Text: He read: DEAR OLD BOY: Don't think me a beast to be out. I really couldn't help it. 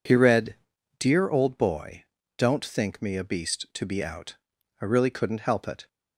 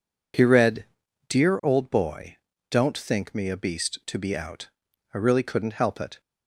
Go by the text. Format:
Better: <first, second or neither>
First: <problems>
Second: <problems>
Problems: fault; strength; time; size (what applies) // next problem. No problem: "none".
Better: neither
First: none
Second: none